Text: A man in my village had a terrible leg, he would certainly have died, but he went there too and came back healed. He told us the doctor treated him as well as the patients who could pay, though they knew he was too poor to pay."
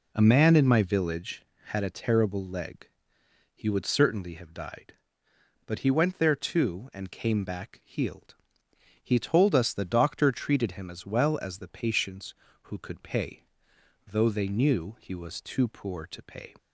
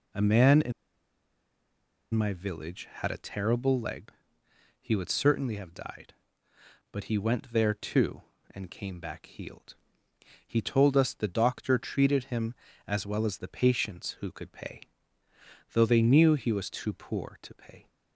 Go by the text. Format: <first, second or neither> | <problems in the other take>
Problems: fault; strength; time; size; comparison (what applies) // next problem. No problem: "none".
first | pauses between "in" and "my"; strong; at 0.7 s; 1.4 s long